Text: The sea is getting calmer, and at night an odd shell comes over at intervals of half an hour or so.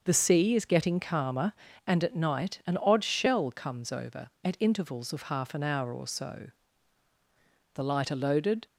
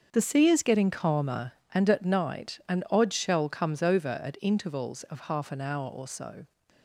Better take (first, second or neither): second